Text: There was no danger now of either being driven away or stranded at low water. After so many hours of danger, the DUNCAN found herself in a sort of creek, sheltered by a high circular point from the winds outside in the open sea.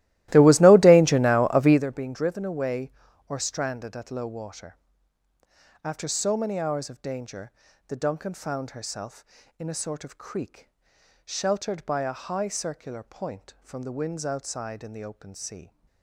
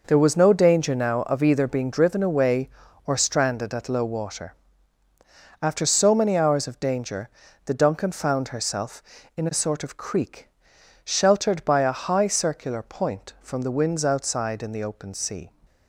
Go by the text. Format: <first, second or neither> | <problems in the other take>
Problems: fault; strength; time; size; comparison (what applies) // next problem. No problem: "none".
second | starts louder than the rest; strong; until 1.8 s; 16.5 dB